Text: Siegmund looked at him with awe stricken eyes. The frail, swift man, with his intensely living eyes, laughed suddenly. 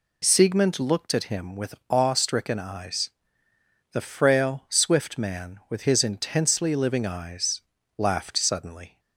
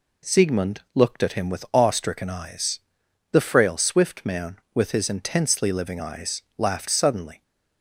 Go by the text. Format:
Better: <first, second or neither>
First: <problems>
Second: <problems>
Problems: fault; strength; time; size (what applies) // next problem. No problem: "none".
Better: neither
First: none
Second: none